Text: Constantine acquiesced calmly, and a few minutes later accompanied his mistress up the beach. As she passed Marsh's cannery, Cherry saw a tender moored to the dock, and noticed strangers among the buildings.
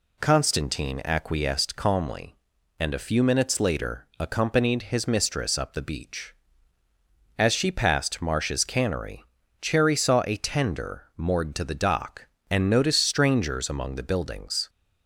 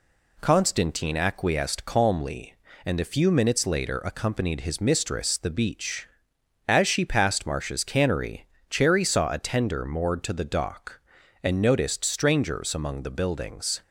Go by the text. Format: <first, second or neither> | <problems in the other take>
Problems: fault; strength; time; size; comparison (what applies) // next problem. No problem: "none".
first | skips "up"; at 5.3 s